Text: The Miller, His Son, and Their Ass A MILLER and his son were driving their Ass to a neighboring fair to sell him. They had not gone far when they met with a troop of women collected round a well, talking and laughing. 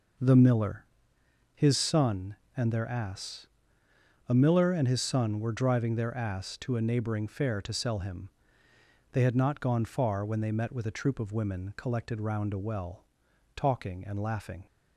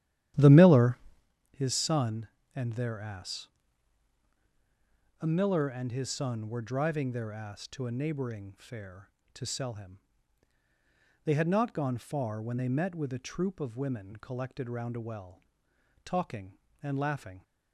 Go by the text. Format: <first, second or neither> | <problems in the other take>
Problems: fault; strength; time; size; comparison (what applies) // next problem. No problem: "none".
first | starts louder than the rest; strong; until 1.3 s; 11.5 dB // pauses between "Ass" and "A"; strong; at 3.4 s; 1.7 s long; noticeable in the first